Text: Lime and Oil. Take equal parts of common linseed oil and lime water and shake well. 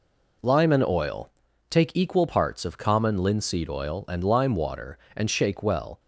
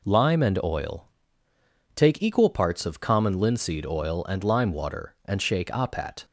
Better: first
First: none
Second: says "apat" for "well"; at 5.6 s

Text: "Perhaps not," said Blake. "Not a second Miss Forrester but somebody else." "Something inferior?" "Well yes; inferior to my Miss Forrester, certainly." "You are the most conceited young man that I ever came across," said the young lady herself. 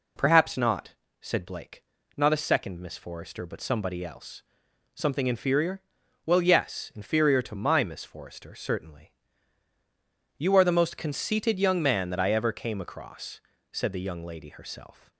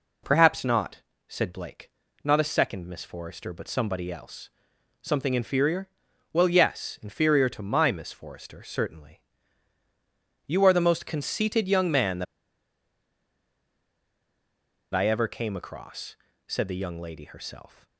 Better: first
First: none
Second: pauses between "that" and "I"; strong; at 12.2 s; 2.6 s long

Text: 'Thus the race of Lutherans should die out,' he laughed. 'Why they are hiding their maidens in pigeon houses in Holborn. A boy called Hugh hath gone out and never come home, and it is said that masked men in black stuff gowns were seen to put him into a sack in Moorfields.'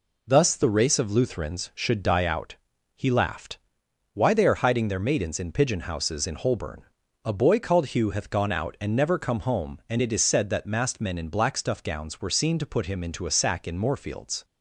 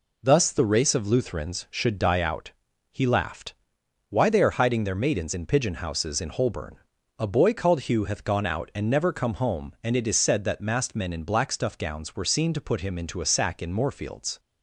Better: neither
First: none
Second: none

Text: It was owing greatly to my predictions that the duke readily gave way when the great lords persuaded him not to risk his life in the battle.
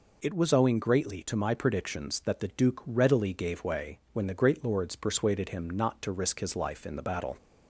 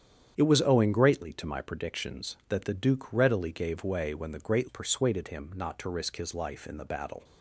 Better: first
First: none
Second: starts louder than the rest; strong; until 1.3 s; 9 dB // skips "lords"; at 4.6 s

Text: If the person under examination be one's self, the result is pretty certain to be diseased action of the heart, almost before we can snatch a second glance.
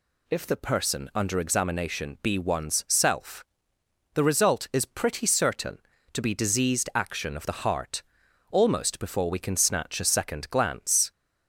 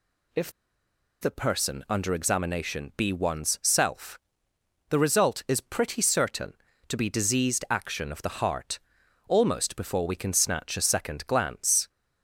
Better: first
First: none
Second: pauses between "If" and "the"; noticeable; at 0.4 s; 0.71 s long

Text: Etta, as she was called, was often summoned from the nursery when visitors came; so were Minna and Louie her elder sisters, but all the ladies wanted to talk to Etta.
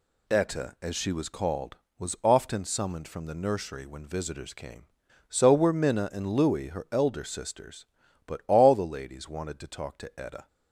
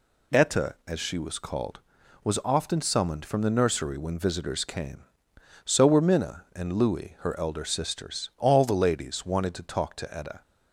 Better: first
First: none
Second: skips "but"; at 8.3 s

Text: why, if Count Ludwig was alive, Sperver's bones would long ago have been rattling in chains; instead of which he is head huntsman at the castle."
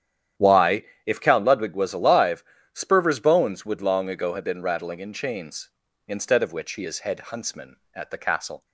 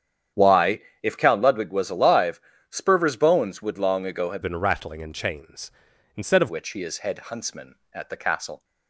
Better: first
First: starts louder than the rest; strong; until 1.6 s; 10 dB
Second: starts louder than the rest; strong; until 1.5 s; 9 dB // changes voice from "been" to "of"; from 4.4 to 6.4 s; 2.0 s long

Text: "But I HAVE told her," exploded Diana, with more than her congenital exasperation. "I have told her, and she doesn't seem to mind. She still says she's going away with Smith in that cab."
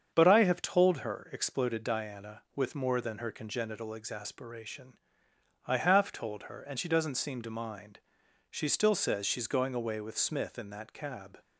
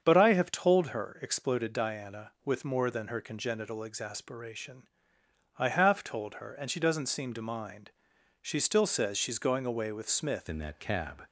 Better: first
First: starts louder than the rest; strong; until 1.1 s; 7.5 dB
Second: starts louder than the rest; strong; until 1.0 s; 7.5 dB // changes voice at "in"; from 10.4 s on; 0.8 s long

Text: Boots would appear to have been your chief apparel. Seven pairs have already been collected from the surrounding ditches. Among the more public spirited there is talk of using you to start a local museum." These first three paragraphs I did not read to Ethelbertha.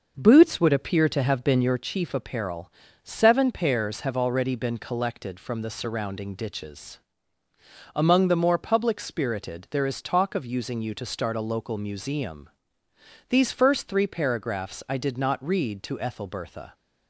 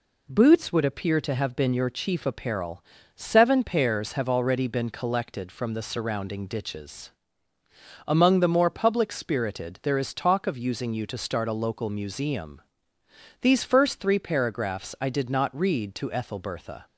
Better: second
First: starts louder than the rest; noticeable; until 1.8 s; 6 dB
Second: none

